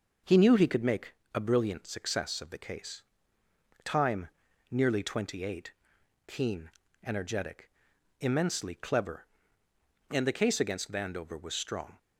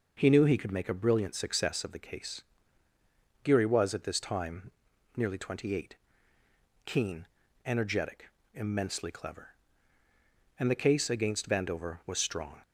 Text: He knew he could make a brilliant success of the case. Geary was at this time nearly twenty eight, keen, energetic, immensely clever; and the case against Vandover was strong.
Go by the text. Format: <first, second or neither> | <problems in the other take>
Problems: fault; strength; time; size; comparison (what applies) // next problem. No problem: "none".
second | pauses between "make" and "a"; slight; at 1.1 s; 0.20 s long // skips "Geary was at this"; at 3.4 s // pauses between "time" and "nearly"; at 4.2 s; 0.44 s long; also in the second